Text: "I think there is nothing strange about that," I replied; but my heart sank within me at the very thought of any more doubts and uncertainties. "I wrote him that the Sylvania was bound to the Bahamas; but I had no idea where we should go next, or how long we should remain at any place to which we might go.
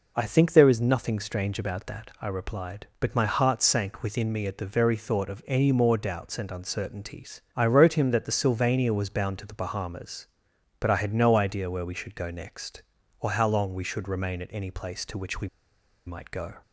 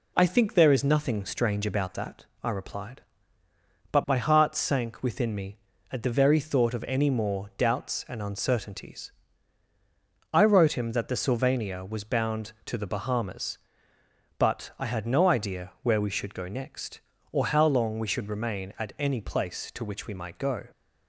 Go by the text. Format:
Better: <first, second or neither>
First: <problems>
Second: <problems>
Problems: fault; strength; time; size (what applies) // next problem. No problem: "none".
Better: second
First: pauses between "we" and "might"; noticeable; at 15.4 s; 0.58 s long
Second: none